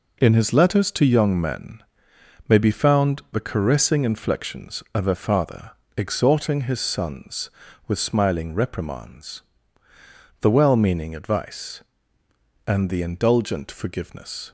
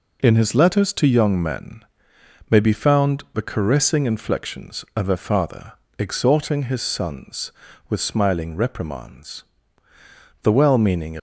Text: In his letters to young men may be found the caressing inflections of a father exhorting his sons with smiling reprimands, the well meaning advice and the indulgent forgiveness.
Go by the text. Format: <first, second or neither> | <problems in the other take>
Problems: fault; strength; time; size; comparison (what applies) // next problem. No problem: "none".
first | pauses between "men" and "may"; noticeable; at 1.8 s; 0.68 s long; noticeable in the first // pauses between "father" and "exhorting"; slight; at 5.7 s; 0.26 s long; slight in the first // stops before "advice and the indulgent forgiveness"; at 11.1 s